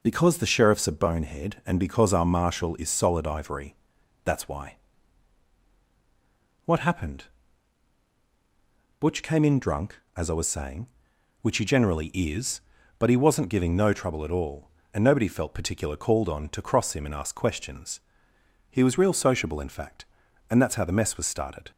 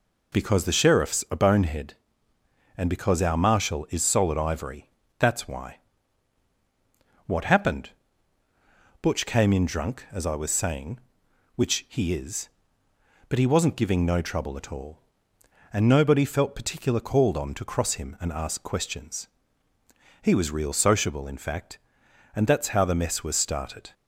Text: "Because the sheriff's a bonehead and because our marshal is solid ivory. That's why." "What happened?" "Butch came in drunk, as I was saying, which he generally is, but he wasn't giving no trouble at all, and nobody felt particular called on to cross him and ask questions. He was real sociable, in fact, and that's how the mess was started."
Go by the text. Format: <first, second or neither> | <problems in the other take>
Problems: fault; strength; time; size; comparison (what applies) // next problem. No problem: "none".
first | skips "generally"; at 12.1 s